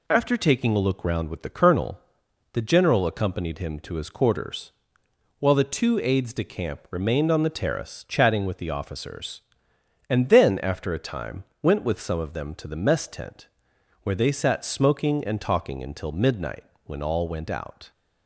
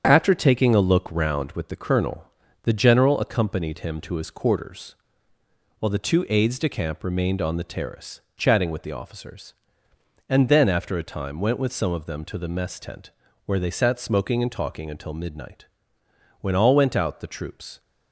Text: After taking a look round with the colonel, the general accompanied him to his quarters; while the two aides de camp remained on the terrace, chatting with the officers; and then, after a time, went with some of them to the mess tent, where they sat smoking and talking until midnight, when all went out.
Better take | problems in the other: first | starts louder than the rest; strong; until 1.0 s; 8 dB // goes on to say "The troops"; from 17.1 s on; 0.60 s long

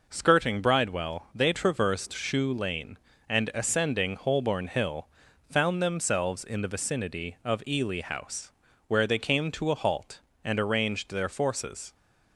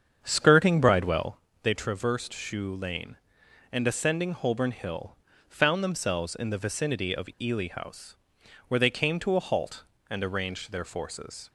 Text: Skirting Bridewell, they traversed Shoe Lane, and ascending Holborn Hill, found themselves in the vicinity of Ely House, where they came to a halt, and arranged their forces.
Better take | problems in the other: first | starts louder than the rest; strong; until 1.4 s; 7.5 dB

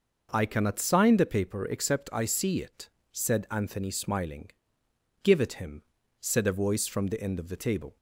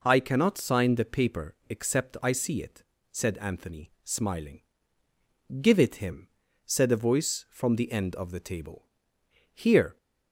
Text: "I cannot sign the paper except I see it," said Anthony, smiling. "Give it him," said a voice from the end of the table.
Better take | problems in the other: first | goes on to say "Here"; slight; from 9.5 s on; 0.44 s long

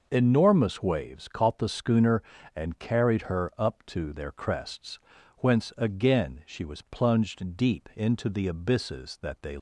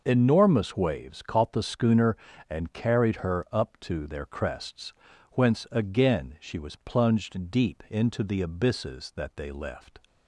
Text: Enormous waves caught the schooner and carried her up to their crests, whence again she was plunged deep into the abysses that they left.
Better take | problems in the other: second | stops before "left"; at 9.5 s

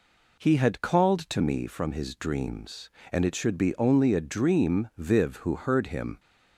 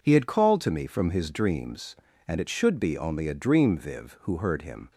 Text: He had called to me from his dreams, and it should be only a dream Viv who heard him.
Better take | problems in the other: neither | none

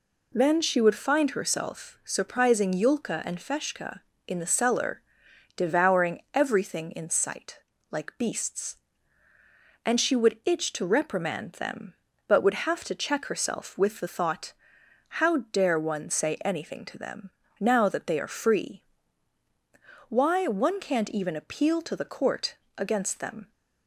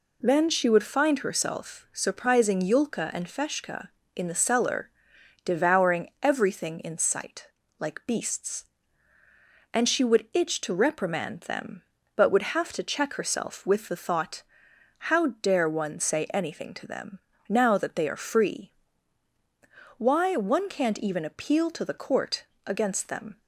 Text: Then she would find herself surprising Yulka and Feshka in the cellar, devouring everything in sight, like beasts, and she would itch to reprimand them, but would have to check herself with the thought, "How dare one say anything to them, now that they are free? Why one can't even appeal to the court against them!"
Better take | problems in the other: neither | pauses between "court" and "against"; slight; the same in both

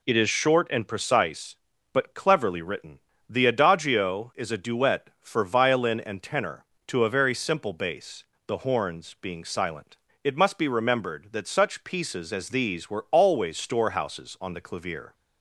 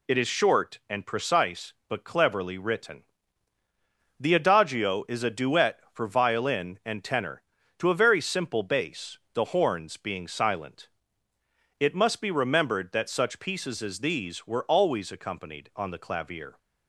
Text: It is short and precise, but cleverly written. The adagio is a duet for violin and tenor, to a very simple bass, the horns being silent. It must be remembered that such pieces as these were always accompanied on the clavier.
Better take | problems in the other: second | says "storehouses" for "accompanied"; at 13.5 s

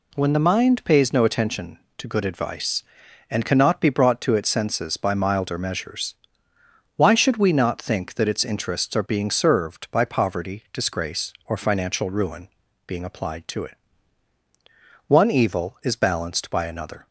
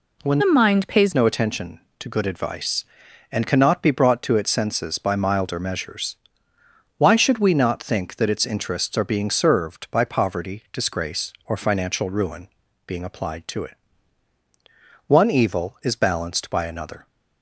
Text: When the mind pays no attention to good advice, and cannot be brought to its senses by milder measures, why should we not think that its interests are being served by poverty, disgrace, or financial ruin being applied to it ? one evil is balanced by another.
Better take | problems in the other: first | changes voice from "the" to "pays"; from 0.3 to 1.1 s; 0.8 s long // pauses between "ruin" and "being"; slight; at 12.4 s; 0.36 s long; slight in the first

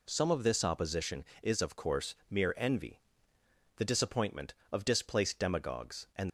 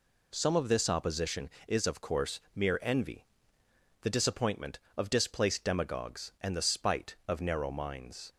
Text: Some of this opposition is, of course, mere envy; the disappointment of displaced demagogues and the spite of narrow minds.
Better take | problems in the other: second | stops before "the spite of narrow minds"; at 6.2 s

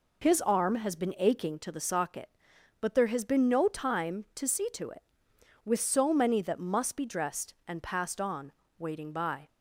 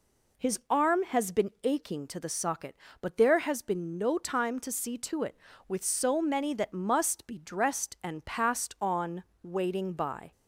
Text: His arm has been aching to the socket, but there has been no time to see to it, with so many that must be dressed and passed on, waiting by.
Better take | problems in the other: neither | none

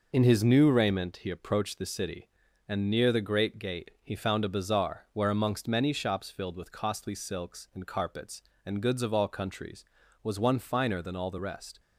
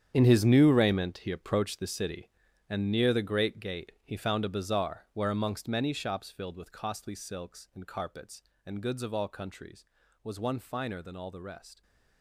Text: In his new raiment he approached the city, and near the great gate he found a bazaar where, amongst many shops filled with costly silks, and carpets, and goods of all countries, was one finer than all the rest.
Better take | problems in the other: first | gets quieter; strong; throughout; 13.5 dB

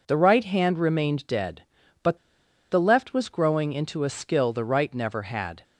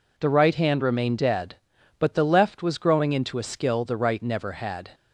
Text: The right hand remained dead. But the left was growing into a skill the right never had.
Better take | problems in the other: second | pauses between "But" and "the"; noticeable; at 2.1 s; 0.53 s long

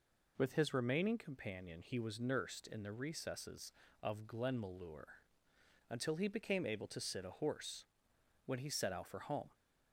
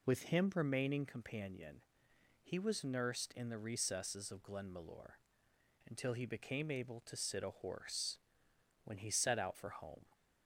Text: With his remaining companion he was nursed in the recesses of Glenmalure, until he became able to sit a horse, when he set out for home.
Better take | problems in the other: first | says "him" for "his"; at 0.2 s // pauses between "companion" and "he"; noticeable; at 1.7 s; 0.64 s long

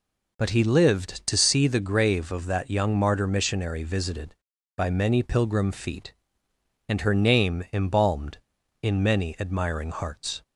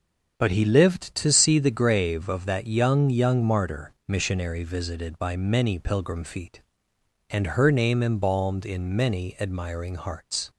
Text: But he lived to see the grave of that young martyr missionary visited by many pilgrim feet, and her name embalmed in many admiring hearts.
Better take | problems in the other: first | starts louder than the rest; until 1.4 s; 7 dB // says "young" twice; at 3.0 s

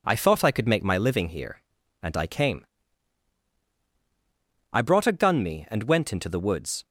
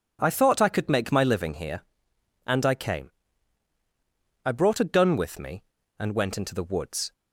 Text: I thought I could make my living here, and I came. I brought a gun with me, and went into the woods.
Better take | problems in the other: second | skips "with"; at 5.4 s

